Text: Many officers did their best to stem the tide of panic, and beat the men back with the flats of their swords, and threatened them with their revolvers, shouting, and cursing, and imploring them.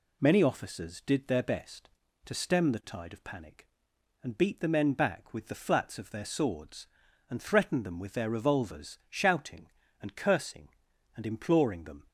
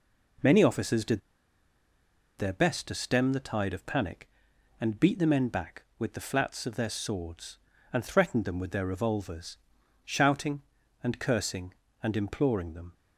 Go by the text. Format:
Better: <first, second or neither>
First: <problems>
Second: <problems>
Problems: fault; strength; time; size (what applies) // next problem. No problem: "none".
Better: first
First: none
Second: pauses between "did" and "their"; at 1.1 s; 1.1 s long